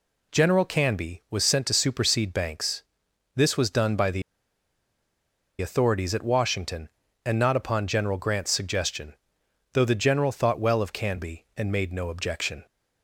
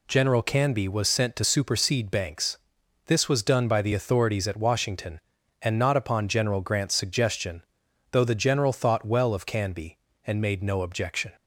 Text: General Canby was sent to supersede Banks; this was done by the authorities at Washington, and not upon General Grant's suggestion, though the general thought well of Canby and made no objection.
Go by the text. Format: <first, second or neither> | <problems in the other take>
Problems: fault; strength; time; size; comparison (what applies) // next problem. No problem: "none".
second | pauses between "the" and "authorities"; strong; at 4.2 s; 1.3 s long